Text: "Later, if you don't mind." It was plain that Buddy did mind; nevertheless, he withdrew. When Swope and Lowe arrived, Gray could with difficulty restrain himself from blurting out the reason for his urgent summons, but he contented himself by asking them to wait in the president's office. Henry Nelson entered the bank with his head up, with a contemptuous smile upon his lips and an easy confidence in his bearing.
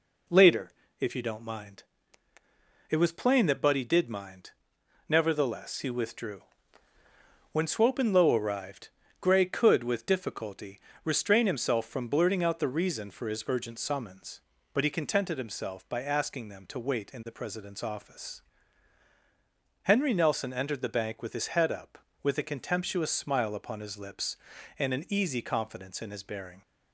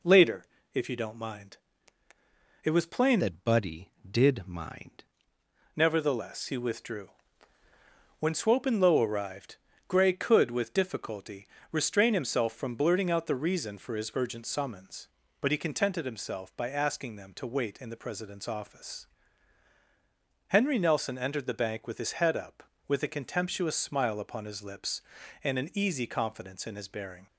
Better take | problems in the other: first | changes voice from "that" to "mind"; from 3.1 to 5.0 s; 1.9 s long // pauses between "difficulty" and "restrain"; slight; at 11.4 s; 0.24 s long; slight in the first

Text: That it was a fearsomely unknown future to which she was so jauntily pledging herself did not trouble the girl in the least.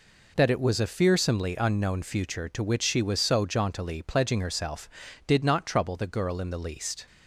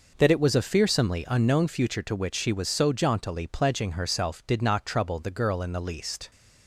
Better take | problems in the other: neither | none

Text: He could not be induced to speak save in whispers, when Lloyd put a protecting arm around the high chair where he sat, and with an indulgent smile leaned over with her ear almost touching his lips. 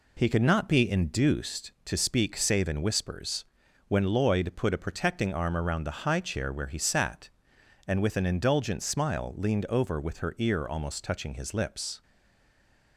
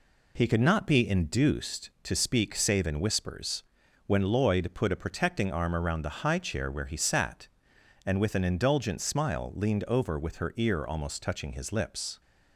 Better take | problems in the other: second | stays silent after the last word; from 12.0 s on; 0.9 s long

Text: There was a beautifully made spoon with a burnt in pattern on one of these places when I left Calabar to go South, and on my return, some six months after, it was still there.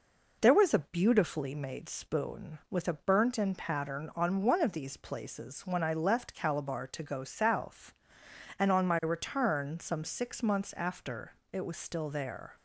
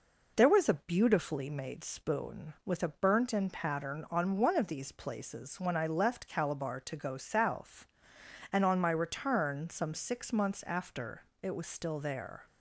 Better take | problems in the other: neither | none

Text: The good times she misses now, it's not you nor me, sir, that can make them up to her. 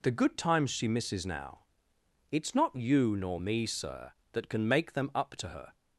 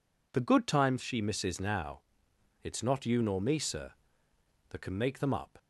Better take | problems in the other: first | stops before "to her"; at 5.5 s

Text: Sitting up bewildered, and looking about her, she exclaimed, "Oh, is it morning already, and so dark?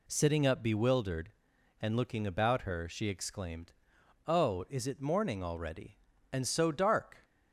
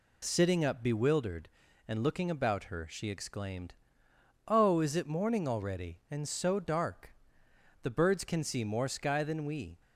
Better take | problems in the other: first | goes on to say "The birds can see more sky than we"; strong; from 7.8 s on; 1.9 s long

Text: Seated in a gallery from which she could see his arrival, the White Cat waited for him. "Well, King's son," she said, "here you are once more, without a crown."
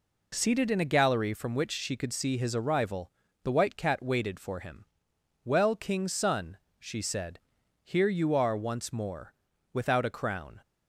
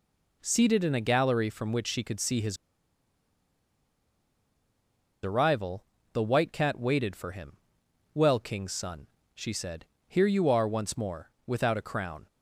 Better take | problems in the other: first | pauses between "his" and "arrival"; strong; at 2.5 s; 2.6 s long

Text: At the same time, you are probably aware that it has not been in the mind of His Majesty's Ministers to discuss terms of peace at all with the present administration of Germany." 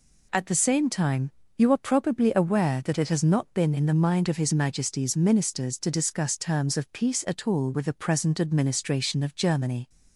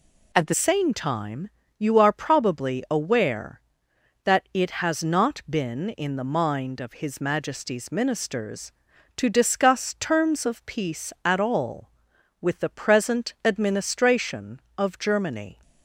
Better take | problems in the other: first | changes voice at "same"; from 0.5 s on; 15.1 s long

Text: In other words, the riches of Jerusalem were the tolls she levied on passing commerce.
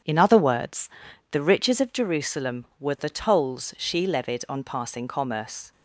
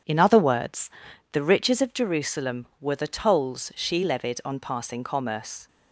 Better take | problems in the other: neither | none

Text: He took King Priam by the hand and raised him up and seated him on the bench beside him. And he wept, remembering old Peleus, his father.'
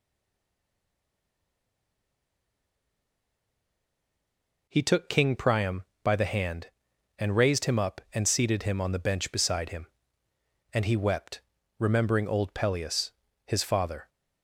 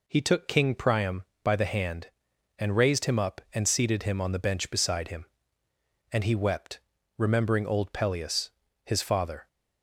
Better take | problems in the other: second | stays silent before the first word; strong; until 4.6 s; 4.6 s long

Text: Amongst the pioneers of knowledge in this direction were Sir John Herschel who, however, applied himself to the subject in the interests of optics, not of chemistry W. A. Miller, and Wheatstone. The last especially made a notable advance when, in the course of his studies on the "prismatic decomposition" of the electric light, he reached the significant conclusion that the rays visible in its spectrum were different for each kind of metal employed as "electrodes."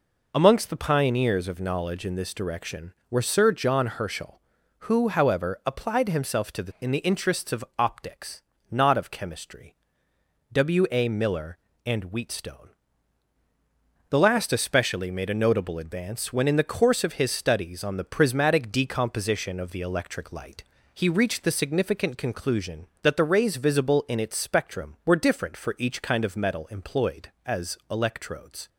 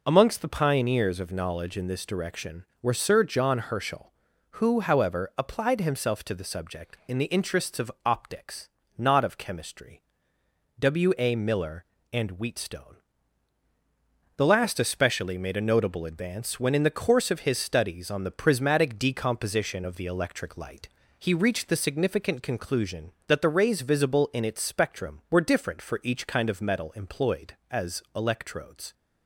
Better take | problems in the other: second | skips "subject"; at 6.7 s // pauses between "chemistry" and "W"; noticeable; at 9.7 s; 0.78 s long; noticeable in the second

